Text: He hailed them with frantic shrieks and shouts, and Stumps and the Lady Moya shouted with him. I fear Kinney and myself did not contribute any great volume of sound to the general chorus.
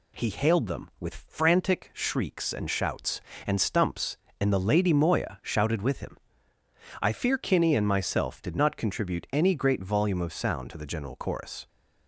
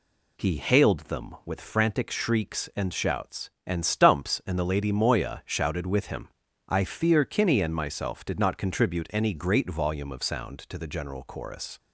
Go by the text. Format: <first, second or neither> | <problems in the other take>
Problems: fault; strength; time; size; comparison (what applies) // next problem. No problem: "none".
neither | none